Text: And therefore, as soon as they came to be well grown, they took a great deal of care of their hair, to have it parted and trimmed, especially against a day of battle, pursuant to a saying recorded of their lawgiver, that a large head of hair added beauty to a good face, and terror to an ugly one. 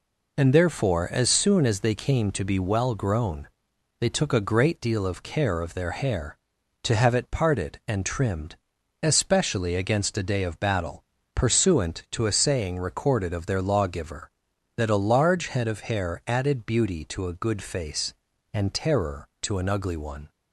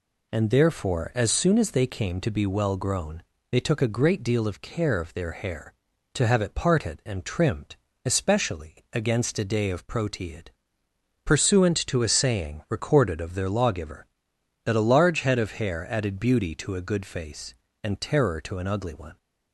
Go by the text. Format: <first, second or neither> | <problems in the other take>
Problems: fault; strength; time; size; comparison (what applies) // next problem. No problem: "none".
first | says "proteid" for "battle"; at 9.8 s